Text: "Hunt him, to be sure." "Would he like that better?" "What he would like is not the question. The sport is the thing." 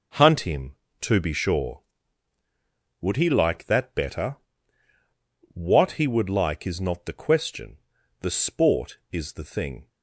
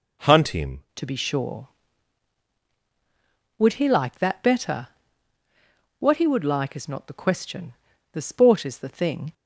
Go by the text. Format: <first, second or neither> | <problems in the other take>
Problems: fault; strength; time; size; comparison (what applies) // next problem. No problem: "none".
first | changes voice at "to"; from 0.9 s on; 8.4 s long